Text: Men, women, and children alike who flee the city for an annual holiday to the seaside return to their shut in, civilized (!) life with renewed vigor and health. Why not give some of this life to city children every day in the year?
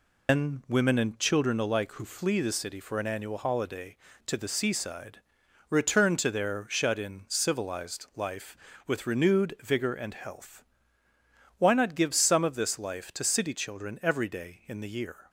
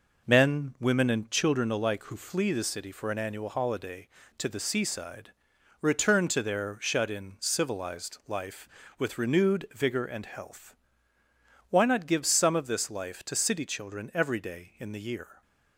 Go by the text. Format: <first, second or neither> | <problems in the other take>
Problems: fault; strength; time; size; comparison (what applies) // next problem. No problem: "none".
second | loses the start of "Men"; at 0.2 s; 155 ms // pauses between "seaside" and "return"; noticeable; at 5.1 s; 0.50 s long; noticeable in the second